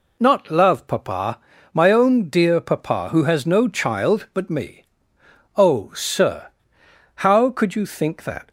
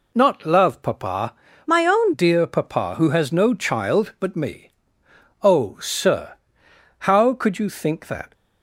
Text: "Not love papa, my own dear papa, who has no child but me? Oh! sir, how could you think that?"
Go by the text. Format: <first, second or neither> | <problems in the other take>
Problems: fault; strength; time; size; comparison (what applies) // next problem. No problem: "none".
first | changes voice from "my" to "own"; from 1.6 to 2.1 s; 0.5 s long